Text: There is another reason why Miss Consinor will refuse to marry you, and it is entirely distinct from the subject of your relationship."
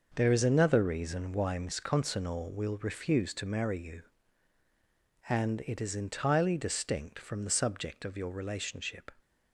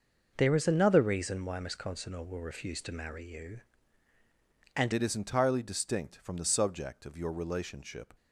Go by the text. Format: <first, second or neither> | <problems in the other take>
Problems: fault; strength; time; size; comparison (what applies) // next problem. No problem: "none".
first | changes voice at "it"; from 4.9 s on; 3.2 s long